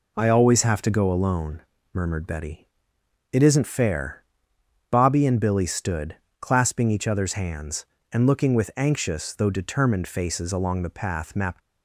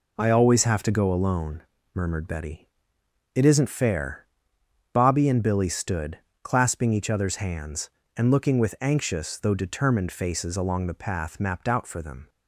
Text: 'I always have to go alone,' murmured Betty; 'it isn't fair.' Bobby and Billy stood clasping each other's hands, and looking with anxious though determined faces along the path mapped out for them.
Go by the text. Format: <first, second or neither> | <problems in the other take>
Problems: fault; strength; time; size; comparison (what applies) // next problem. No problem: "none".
second | pauses between "stood" and "clasping"; slight; at 6.1 s; 0.24 s long; slight in the second // stops before "out for them"; at 11.6 s